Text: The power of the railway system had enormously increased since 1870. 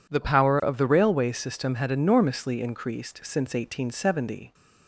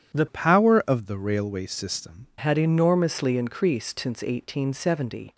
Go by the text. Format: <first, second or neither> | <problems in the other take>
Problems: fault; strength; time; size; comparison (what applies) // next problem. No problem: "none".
first | starts louder than the rest; strong; until 1.2 s; 9.5 dB // changes voice from "power" to "system"; from 0.2 to 2.2 s; 2.0 s long